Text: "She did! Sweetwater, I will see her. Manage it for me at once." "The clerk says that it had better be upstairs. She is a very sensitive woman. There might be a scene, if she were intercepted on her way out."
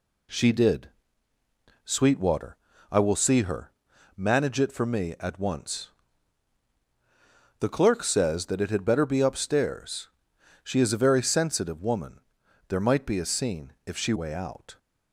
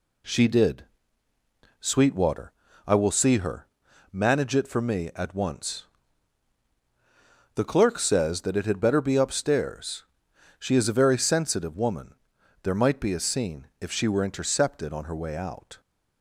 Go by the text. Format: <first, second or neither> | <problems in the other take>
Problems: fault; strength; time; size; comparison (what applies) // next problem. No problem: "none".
second | skips "were intercepted on her"; at 14.1 s